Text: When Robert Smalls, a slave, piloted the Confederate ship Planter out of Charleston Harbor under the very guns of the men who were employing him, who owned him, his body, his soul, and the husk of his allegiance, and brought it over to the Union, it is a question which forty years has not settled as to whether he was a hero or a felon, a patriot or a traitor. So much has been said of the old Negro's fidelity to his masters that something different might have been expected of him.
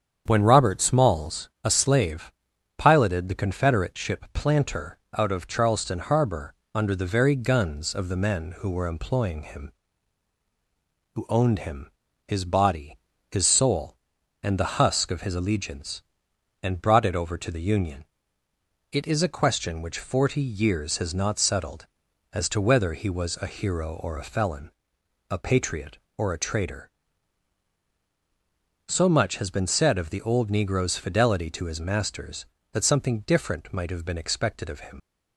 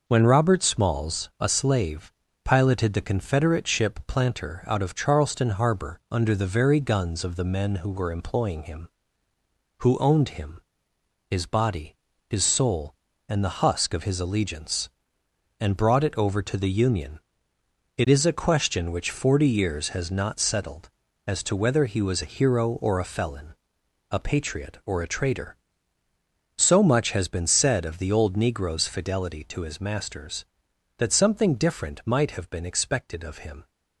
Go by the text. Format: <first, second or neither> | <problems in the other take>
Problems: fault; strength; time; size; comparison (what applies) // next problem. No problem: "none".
second | starts louder than the rest; strong; until 1.2 s; 8 dB // pauses between "Planter" and "out"; slight; at 4.9 s; 0.20 s long // pauses between "Harbor" and "under"; slight; at 6.5 s; 0.22 s long // leaves "him" unfinished; at 34.9 s; 55 ms